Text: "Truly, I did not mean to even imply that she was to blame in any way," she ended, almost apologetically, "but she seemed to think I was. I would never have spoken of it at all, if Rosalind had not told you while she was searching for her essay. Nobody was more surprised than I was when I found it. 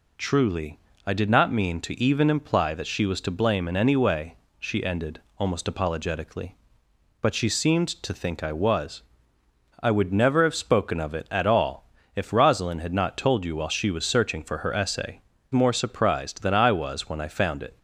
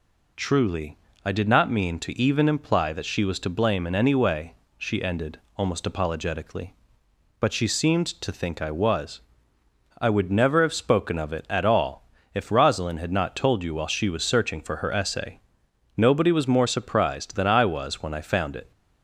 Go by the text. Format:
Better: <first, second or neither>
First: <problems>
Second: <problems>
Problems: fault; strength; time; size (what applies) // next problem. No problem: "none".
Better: second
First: skips "Nobody was"; at 15.3 s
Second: none